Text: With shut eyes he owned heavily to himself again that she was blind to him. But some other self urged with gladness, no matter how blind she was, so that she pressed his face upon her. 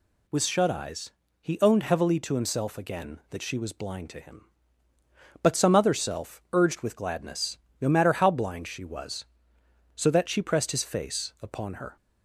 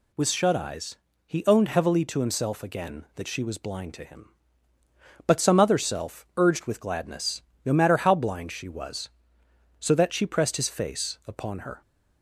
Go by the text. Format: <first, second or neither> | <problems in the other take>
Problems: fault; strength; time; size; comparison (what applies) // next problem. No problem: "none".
neither | pauses between "eyes" and "he"; slight; the same in both